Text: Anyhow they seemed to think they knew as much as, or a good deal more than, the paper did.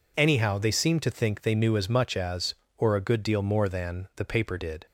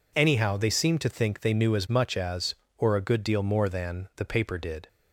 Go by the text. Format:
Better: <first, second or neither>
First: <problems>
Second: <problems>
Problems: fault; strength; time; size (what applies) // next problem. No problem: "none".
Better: neither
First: none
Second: none